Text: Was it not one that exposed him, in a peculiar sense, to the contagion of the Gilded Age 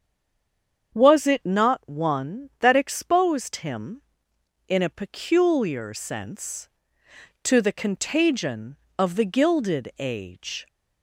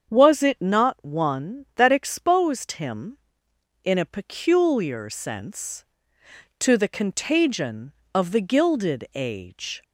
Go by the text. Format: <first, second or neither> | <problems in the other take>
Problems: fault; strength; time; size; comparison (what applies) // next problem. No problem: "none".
second | stays silent before the first word; slight; until 0.9 s; 0.9 s long // starts louder than the rest; strong; until 2.0 s; 7.5 dB; strong in the second